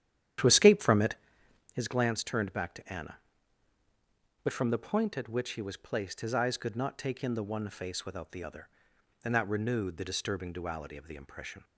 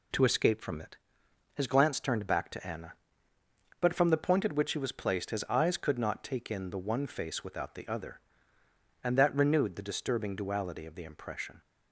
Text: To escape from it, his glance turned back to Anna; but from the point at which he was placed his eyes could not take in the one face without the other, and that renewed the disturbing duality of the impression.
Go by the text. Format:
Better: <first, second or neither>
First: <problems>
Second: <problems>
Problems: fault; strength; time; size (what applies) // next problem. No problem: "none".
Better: second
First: starts louder than the rest; strong; until 1.7 s; 10 dB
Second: none